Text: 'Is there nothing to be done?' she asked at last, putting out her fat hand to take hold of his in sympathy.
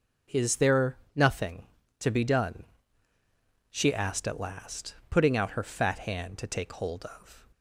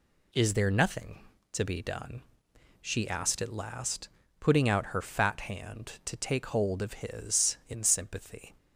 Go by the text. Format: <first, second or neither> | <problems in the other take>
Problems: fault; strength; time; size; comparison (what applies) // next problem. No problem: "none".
second | pauses between "there" and "nothing"; slight; at 0.9 s; 0.18 s long // stops before "his in sympathy"; at 7.5 s